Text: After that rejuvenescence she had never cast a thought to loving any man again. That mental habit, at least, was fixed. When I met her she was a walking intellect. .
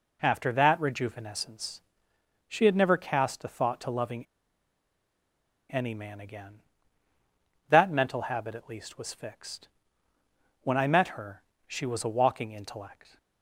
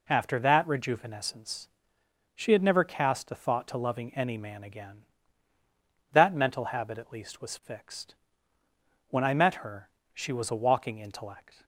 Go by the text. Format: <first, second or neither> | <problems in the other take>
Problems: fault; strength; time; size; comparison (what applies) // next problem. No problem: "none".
second | pauses between "rejuvenescence" and "she"; noticeable; at 1.8 s; 0.66 s long; noticeable in the second // pauses between "loving" and "any"; strong; at 4.2 s; 1.4 s long // pauses between "her" and "she"; slight; at 11.4 s; 0.24 s long; slight in the second